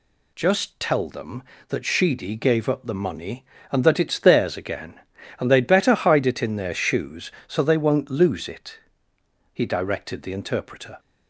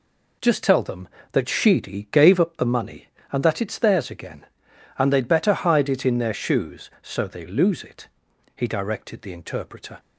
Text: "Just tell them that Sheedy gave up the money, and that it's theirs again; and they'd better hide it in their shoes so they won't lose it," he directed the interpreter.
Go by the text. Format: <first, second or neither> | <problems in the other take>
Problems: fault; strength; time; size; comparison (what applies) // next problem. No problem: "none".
first | skips "won't"; at 7.4 s